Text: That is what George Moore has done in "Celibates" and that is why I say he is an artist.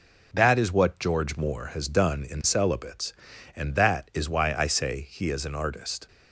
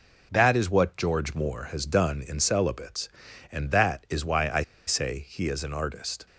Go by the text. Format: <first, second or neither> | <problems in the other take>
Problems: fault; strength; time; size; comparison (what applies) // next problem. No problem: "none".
first | pauses between "I" and "say"; slight; at 4.6 s; 0.24 s long